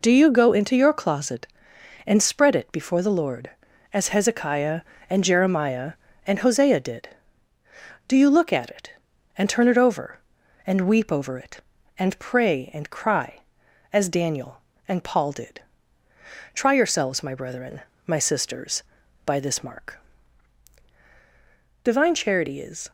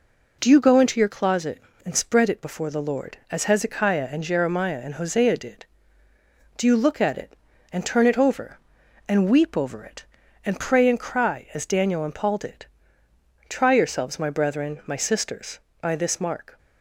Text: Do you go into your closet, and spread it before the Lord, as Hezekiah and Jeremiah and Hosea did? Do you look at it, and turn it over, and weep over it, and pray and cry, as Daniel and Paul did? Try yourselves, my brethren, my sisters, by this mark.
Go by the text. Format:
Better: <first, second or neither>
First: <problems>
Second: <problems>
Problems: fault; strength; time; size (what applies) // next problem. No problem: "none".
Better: second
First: goes on to say "Divine Charity is"; noticeable; from 21.8 s on; 1.0 s long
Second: none